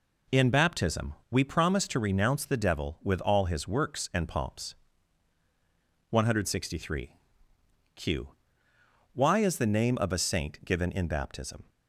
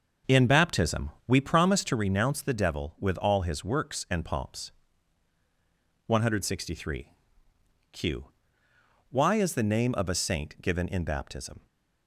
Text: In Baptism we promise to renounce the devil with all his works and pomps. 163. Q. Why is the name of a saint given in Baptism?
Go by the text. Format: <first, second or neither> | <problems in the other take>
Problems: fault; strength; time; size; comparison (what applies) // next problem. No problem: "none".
first | starts louder than the rest; until 2.1 s; 6.5 dB // pauses between "Baptism" and "we"; slight; at 1.1 s; 0.16 s long; slight in the first